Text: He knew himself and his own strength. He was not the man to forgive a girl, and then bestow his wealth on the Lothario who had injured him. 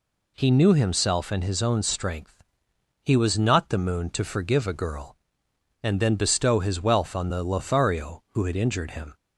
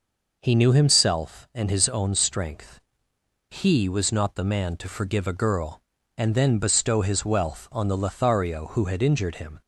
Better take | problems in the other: second | says "moon" for "man"; at 3.7 s

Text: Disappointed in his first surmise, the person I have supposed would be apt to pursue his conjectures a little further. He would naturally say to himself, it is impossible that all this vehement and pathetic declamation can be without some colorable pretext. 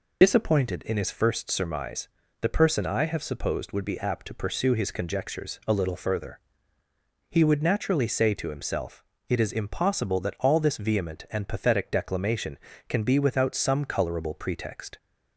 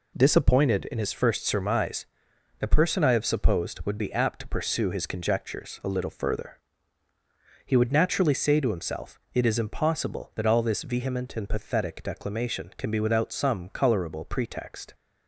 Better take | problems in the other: second | loses the start of "Disappointed"; at 0.2 s; 55 ms

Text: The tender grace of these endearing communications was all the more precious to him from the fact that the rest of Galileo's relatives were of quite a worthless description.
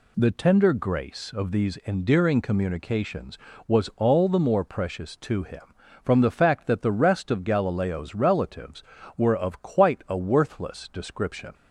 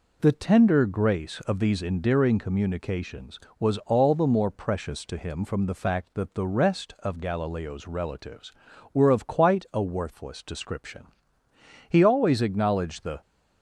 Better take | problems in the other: first | goes on to say "He always acknowledged the"; from 11.8 s on; 1.3 s long

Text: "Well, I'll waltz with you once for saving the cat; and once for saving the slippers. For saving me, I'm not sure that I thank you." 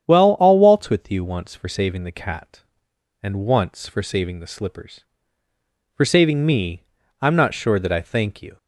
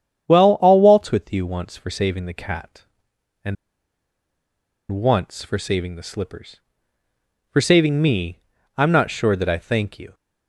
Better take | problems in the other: first | starts louder than the rest; strong; until 1.3 s; 9 dB; strong in the first // pauses between "and" and "once"; strong; at 3.5 s; 1.3 s long

